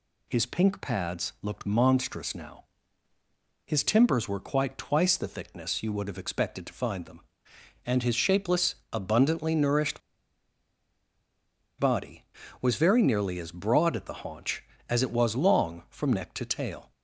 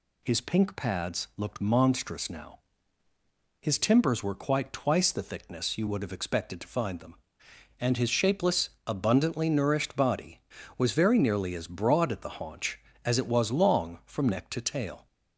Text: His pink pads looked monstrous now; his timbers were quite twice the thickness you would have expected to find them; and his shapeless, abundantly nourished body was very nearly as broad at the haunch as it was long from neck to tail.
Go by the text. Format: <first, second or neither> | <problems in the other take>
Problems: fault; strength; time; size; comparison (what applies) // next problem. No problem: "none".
second | pauses between "nourished" and "body"; strong; at 10.0 s; 1.8 s long